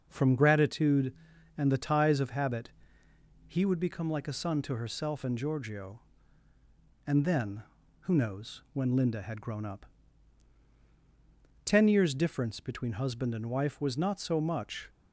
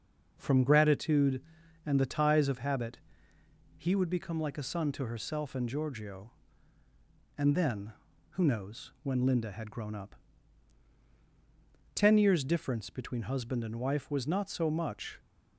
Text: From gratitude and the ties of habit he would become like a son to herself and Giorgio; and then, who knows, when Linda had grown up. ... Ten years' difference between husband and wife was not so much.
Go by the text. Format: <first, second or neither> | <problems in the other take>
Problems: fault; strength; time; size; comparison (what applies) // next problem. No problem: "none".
neither | pauses between "habit" and "he"; noticeable; the same in both